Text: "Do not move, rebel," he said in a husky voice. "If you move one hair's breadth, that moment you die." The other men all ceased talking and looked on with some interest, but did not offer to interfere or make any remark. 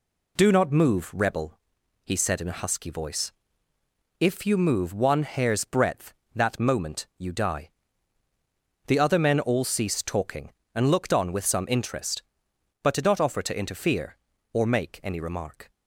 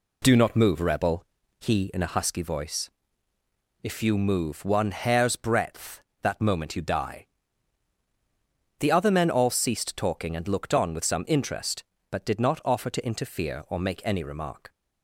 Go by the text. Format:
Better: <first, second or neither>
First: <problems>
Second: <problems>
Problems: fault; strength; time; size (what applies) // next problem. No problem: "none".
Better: first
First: none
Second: skips "said"; at 1.9 s